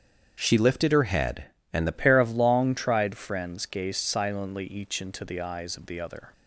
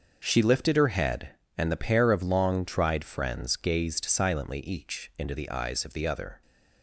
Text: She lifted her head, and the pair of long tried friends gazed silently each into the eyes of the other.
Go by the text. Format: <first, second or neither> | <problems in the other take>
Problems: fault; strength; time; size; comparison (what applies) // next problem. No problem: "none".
second | starts louder than the rest; strong; until 1.4 s; 8 dB; also in the second // changes voice at "pair"; from 1.9 s on; 4.4 s long